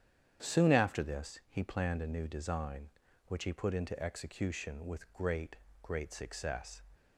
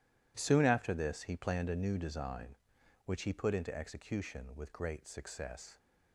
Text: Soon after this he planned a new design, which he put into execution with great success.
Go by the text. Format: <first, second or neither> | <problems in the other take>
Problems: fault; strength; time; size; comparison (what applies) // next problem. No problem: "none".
second | starts louder than the rest; strong; until 1.5 s; 9 dB // says "great" twice; at 5.8 s